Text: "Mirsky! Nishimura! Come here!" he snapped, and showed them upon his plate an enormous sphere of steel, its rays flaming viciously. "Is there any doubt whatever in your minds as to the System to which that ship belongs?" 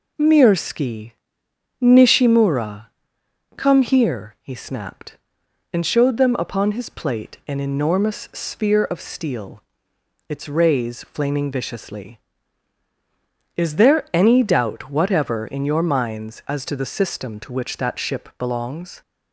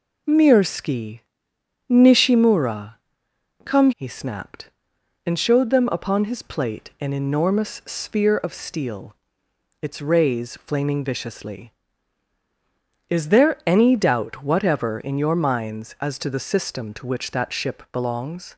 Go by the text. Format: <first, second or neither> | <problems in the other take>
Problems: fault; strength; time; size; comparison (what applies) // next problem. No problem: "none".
first | skips "here"; at 3.9 s